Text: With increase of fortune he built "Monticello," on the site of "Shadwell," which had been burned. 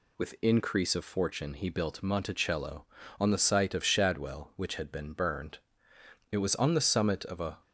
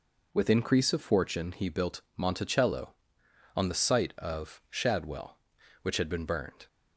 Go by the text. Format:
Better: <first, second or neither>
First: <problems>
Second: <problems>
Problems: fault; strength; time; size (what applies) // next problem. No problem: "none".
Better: second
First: goes on to say "It was on the summit of a"; noticeable; from 6.3 s on; 1.2 s long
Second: none